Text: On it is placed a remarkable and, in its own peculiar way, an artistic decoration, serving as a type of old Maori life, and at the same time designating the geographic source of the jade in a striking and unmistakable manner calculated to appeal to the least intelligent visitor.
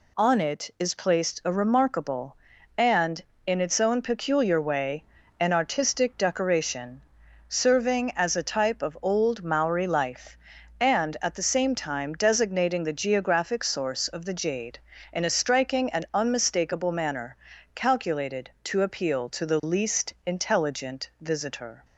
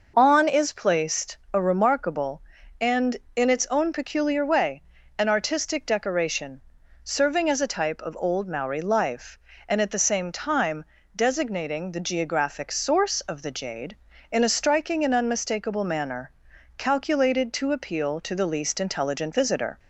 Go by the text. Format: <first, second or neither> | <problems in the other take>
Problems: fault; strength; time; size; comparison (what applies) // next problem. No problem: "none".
first | skips "it"; at 0.4 s // pauses between "time" and "designating"; slight; at 10.8 s; 0.32 s long // pauses between "manner" and "calculated"; at 16.3 s; 0.44 s long; also in the first